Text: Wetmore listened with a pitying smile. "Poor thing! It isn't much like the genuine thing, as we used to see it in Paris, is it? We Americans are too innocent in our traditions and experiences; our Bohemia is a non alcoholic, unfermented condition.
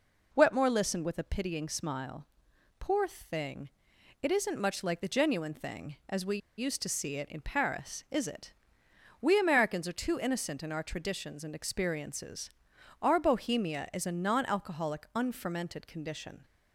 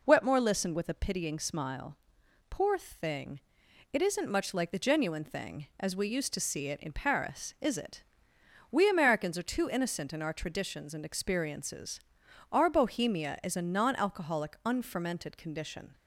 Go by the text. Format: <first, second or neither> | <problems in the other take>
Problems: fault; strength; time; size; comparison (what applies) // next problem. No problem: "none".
second | pauses between "we" and "used"; slight; at 6.3 s; 0.20 s long